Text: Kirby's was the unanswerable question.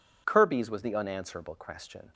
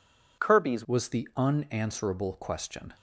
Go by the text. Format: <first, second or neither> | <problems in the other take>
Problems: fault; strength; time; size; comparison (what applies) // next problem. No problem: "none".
first | changes voice at "was"; from 0.8 s on; 2.1 s long